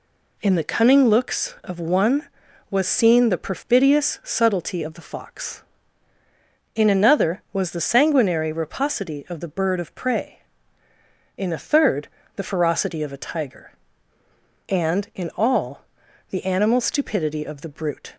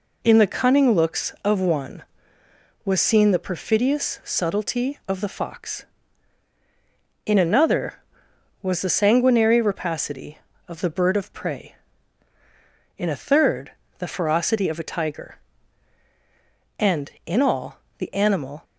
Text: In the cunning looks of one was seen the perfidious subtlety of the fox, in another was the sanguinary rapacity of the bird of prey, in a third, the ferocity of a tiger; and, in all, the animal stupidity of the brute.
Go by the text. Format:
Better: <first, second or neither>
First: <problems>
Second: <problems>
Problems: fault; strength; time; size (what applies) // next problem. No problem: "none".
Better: first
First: none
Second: stops before "stupidity of the brute"; at 18.6 s